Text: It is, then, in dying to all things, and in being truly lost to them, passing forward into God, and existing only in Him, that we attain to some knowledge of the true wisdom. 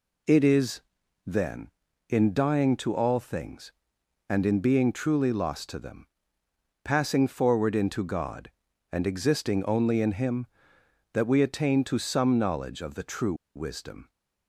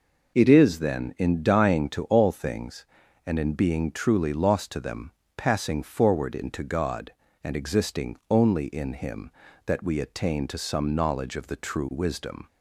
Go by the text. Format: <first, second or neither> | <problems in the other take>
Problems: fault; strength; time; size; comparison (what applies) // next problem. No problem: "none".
second | pauses between "true" and "wisdom"; slight; at 13.3 s; 0.21 s long